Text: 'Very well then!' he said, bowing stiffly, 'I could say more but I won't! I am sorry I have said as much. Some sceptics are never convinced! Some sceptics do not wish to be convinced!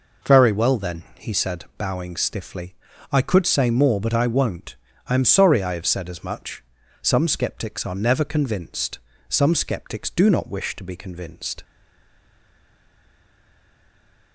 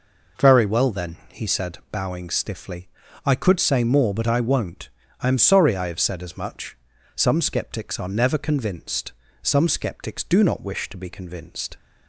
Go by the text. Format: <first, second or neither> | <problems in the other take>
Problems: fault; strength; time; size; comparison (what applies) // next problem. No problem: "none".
second | stays silent after the last word; strong; from 11.6 s on; 2.7 s long